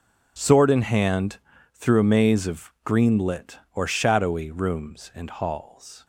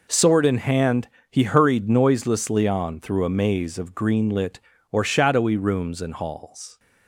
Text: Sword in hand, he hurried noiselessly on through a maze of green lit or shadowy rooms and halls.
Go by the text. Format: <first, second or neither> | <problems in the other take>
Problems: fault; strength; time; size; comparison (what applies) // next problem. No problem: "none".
second | skips "he hurried noiselessly on"; at 1.5 s